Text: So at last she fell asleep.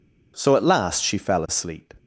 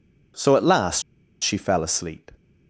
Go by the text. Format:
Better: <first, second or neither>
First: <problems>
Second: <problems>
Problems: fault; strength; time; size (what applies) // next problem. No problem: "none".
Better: first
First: none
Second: pauses between "last" and "she"; at 1.0 s; 0.40 s long